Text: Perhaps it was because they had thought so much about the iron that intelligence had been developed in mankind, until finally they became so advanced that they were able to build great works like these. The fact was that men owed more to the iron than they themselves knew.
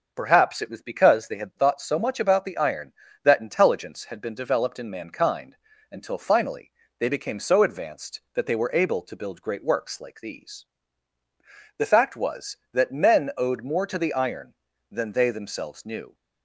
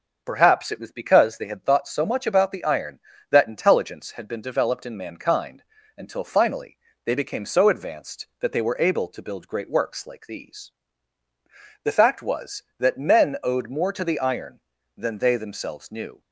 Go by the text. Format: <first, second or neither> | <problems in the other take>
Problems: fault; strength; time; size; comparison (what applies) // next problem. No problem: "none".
neither | starts louder than the rest; the same in both // pauses between "finally" and "they"; slight; the same in both